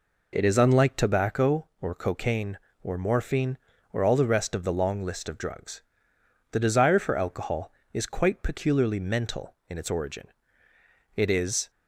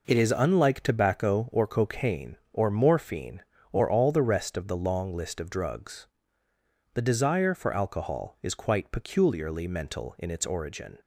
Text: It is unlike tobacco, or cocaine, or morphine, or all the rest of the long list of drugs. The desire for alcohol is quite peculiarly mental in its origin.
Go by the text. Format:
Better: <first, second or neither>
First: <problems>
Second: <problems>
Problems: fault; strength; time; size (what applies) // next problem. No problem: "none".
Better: second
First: goes on to say "It is"; from 11.1 s on; 0.54 s long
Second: none